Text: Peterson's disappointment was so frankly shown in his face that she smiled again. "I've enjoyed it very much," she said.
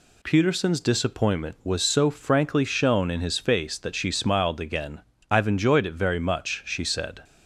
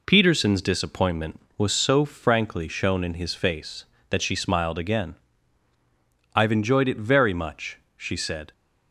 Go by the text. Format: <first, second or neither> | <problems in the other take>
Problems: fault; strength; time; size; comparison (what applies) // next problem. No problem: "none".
neither | none